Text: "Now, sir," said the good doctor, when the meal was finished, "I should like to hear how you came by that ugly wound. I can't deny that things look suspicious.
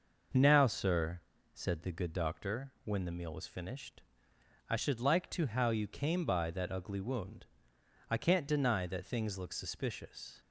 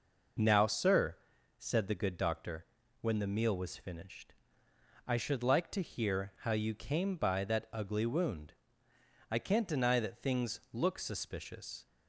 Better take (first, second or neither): second